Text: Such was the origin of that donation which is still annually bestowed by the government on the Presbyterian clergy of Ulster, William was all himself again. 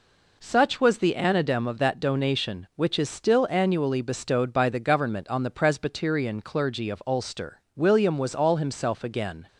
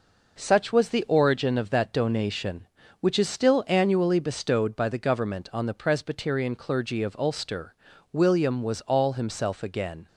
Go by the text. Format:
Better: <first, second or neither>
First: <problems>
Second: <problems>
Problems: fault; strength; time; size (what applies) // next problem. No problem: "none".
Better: second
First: says "anadem" for "origin"; at 1.1 s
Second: none